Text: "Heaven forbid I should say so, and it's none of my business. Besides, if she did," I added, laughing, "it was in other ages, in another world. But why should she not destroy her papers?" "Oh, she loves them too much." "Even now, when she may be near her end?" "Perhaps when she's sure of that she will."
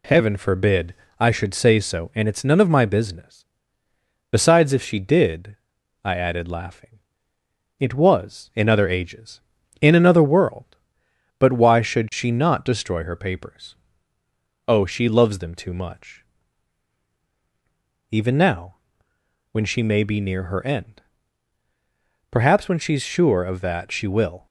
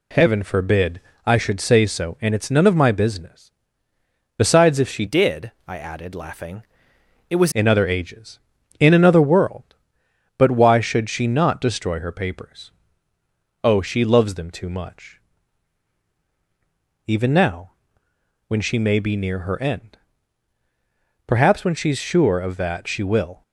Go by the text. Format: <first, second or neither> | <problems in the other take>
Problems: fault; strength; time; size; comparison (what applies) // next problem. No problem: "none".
first | pauses between "forbid" and "I"; slight; at 0.9 s; 0.26 s long; slight in the first // changes voice from "did" to "was"; from 5.0 to 7.5 s; 2.5 s long